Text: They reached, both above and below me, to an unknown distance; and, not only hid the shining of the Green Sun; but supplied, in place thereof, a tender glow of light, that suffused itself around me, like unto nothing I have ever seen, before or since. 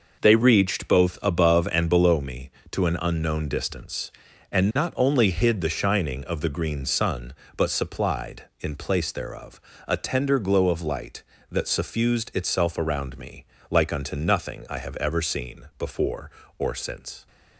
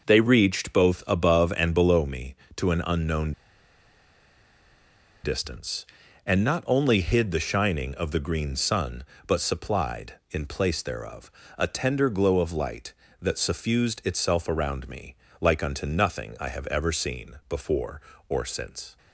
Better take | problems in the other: first | pauses between "unknown" and "distance"; strong; at 3.3 s; 1.9 s long

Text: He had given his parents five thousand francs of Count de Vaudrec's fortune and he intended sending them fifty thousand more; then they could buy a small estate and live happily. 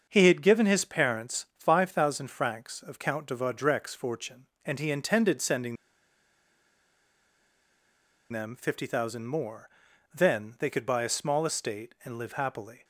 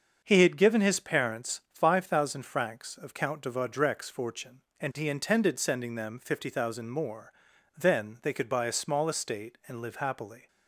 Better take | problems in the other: second | starts louder than the rest; until 1.1 s; 6.5 dB; also in the second // pauses between "sending" and "them"; strong; at 5.7 s; 2.5 s long

